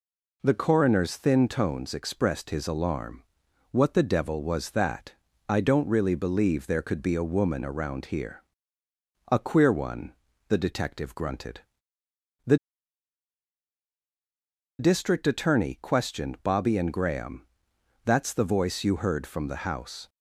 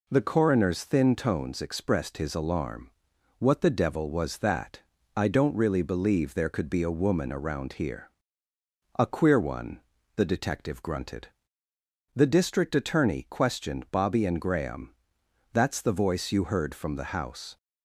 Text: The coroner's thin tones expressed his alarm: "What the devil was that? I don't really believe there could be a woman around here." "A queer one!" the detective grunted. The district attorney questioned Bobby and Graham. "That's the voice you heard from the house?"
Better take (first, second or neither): second